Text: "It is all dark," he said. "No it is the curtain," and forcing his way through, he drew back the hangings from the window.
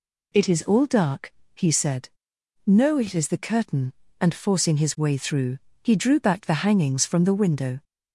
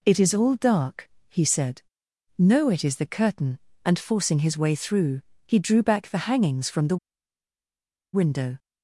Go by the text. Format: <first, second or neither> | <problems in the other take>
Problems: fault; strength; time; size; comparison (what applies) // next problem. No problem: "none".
first | pauses between "the" and "window"; at 6.9 s; 1.1 s long